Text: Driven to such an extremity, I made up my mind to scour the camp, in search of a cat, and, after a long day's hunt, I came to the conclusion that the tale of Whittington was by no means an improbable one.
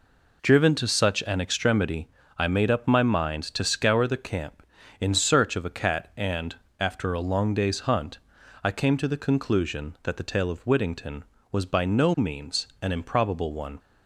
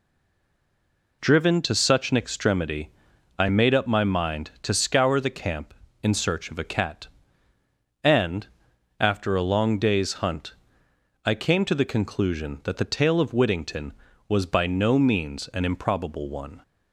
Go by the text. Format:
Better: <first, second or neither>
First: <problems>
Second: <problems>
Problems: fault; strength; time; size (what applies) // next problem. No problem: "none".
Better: first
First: none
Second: stays silent before the first word; noticeable; until 1.2 s; 1.2 s long